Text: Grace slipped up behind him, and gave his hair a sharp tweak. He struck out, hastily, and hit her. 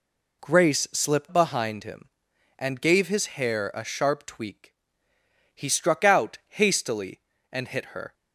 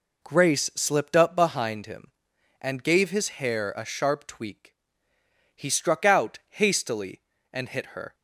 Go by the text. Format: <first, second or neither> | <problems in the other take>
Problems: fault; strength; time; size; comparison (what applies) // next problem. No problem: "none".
second | skips "up"; at 1.3 s